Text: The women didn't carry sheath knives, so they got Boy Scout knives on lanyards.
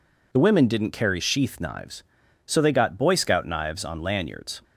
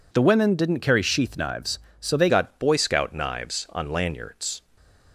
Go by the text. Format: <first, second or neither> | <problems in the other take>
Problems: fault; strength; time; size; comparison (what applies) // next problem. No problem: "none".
first | changes voice at "got"; from 2.2 s on; 2.4 s long // stays silent after the last word; slight; from 4.5 s on; 0.6 s long